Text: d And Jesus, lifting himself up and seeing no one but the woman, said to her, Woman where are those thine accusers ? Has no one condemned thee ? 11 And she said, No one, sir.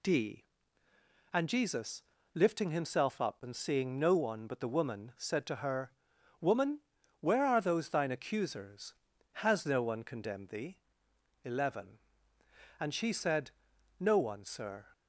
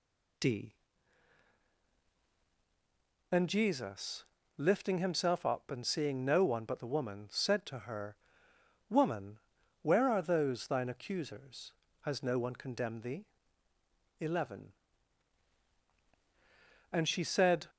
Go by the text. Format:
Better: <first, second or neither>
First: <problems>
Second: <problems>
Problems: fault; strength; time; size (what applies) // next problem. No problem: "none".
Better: first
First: pauses between "Woman" and "where"; at 6.7 s; 0.42 s long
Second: pauses between "Woman" and "where"; at 9.3 s; 0.44 s long // stops before "No one sir"; at 17.6 s